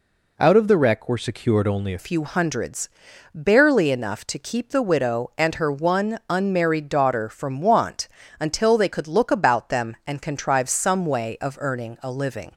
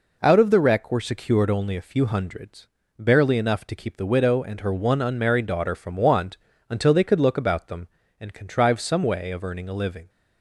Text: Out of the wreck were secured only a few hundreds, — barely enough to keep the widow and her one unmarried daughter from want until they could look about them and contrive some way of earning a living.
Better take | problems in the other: second | changes voice at "few"; from 1.9 s on; 10.6 s long // pauses between "want" and "until"; slight; at 8.0 s; 0.32 s long; slight in the second

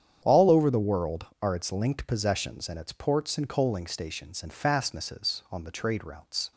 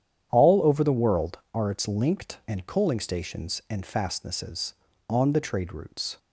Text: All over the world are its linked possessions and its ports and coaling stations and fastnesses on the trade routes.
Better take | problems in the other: first | starts louder than the rest; strong; until 1.3 s; 9.5 dB; strong in the first // skips "possessions and its ports"; at 2.4 s

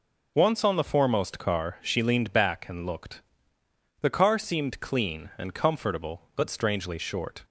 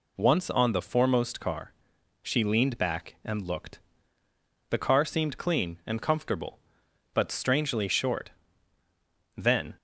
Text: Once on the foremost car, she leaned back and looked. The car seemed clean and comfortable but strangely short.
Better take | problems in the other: first | goes on to say "Then"; slight; from 9.3 s on; 0.38 s long

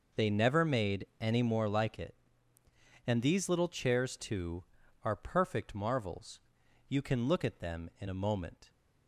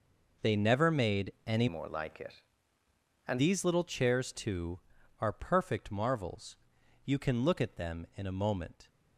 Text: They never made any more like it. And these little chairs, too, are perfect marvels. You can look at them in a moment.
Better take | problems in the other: first | changes voice from "more" to "And"; from 1.6 to 3.3 s; 1.7 s long

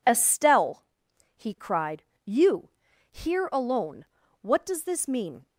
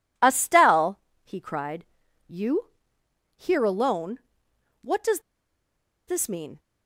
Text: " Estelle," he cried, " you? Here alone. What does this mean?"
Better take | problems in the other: first | pauses between "does" and "this"; noticeable; at 5.1 s; 0.87 s long

